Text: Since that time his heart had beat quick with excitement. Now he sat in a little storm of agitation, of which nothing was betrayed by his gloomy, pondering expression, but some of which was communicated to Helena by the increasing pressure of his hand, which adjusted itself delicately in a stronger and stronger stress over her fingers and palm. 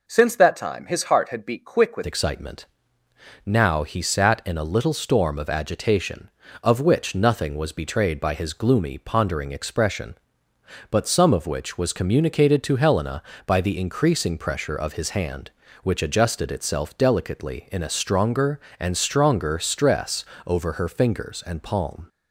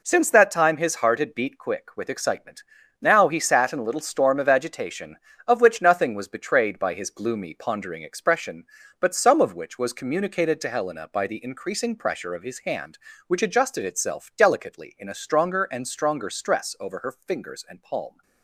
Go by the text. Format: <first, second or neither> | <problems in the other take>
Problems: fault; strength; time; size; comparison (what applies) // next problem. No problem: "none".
second | changes voice at "excitement"; from 2.0 s on; 20.0 s long // pauses between "stress" and "over"; slight; at 20.2 s; 0.22 s long